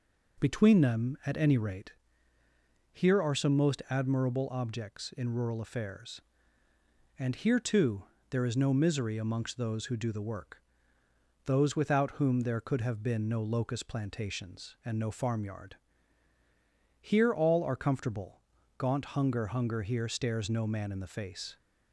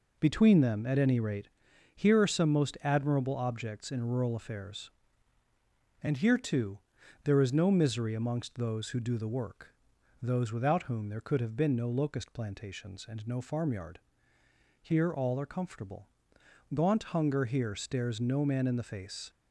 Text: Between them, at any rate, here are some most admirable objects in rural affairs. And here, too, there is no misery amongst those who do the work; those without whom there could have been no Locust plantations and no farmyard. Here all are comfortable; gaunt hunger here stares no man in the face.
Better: second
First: says "hunger" twice; at 19.4 s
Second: none

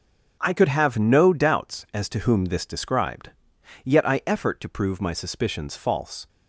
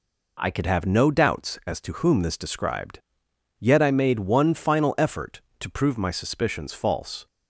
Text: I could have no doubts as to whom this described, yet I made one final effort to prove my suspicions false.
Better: second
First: starts louder than the rest; until 1.4 s; 7 dB // skips "made one final"; at 4.2 s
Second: none

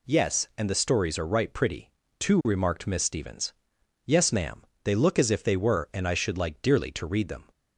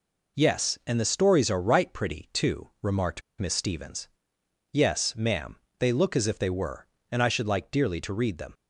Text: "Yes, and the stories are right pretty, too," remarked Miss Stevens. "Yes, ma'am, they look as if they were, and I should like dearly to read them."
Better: first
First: none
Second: pauses between "remarked" and "Miss"; slight; at 3.2 s; 0.18 s long

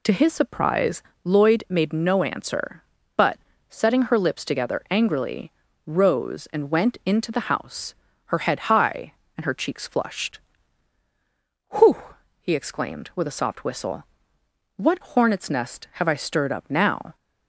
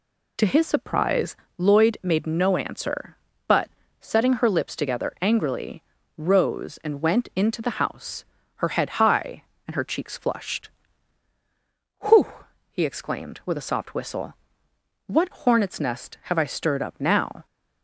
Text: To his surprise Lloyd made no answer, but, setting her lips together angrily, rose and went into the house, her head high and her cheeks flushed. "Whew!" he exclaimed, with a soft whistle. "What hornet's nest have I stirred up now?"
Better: neither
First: pauses between "surprise" and "Lloyd"; slight; at 1.0 s; 0.22 s long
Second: pauses between "surprise" and "Lloyd"; slight; at 1.3 s; 0.22 s long

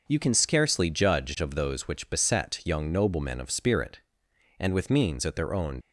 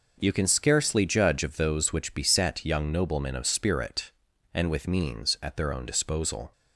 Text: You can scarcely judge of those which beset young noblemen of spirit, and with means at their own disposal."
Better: second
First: stops before "disposal"; at 5.8 s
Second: none

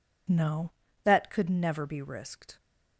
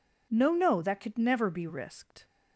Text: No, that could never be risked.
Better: first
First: none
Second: says "No" twice; at 0.5 s

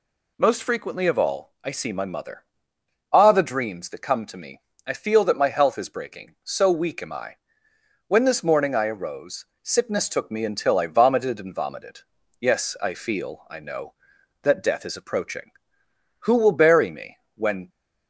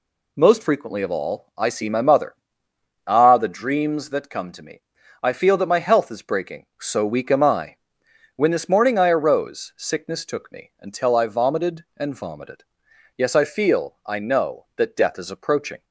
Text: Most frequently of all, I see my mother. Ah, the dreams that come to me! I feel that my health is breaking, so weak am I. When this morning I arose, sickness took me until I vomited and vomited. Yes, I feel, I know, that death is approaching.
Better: second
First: goes on to say "Who will bury me when"; from 16.2 s on; 1.4 s long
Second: none

